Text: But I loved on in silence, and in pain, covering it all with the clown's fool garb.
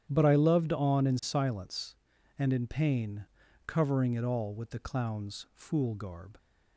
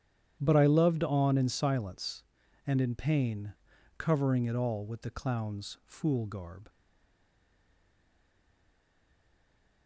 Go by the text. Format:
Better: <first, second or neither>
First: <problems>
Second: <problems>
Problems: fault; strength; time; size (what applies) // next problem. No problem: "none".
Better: first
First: starts louder than the rest; strong; until 1.0 s; 10 dB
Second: starts louder than the rest; strong; until 1.4 s; 10 dB // stays silent after the last word; strong; from 6.6 s on; 3.2 s long